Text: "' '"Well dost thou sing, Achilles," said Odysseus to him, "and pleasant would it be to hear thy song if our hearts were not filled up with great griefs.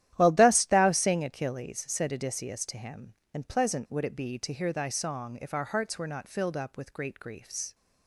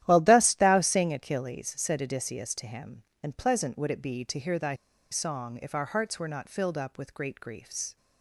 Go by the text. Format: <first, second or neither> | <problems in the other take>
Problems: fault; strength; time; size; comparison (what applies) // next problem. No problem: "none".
first | starts louder than the rest; strong; until 1.0 s; 12.5 dB; strong in the first // pauses between "thy" and "song"; at 4.7 s; 0.36 s long